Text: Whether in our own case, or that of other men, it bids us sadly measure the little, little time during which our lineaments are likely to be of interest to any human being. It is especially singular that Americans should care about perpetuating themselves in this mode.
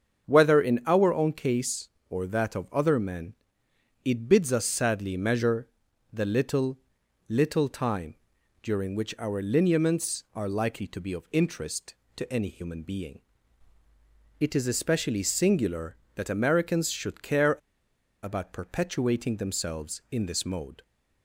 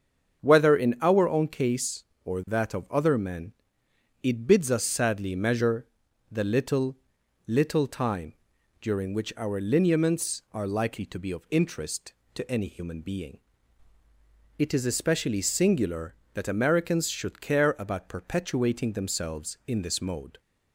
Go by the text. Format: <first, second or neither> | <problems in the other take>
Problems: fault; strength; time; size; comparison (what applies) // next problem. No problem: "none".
second | starts louder than the rest; until 1.3 s; 7 dB; strong in the second // pauses between "measure" and "the"; noticeable; at 5.6 s; 0.46 s long; noticeable in the second // pauses between "time" and "during"; noticeable; at 8.1 s; 0.48 s long; noticeable in the second // pauses between "care" and "about"; noticeable; at 17.5 s; 0.66 s long